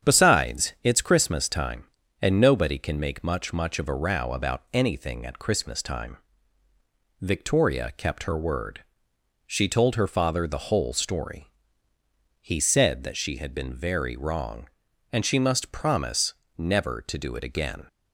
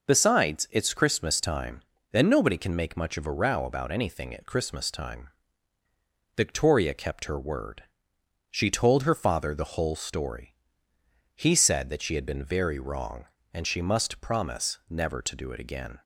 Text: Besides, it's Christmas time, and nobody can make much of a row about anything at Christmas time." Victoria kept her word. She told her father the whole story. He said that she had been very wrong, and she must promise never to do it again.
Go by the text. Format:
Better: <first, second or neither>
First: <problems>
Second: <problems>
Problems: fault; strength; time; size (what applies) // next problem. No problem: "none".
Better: second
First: starts louder than the rest; strong; until 1.1 s; 8.5 dB // says "much" twice; at 3.5 s // pauses between "promise" and "never"; slight; at 16.3 s; 0.24 s long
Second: none